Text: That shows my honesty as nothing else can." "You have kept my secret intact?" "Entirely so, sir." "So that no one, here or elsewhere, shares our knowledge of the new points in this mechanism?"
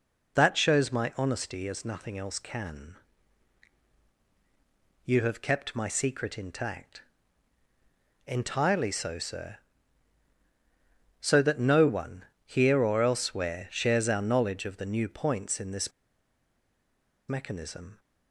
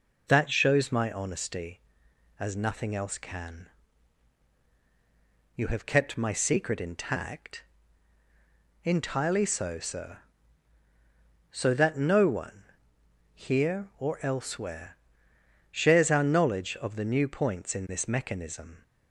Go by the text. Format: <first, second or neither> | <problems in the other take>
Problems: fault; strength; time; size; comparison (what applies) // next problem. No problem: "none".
second | pauses between "this" and "mechanism"; strong; at 15.9 s; 1.3 s long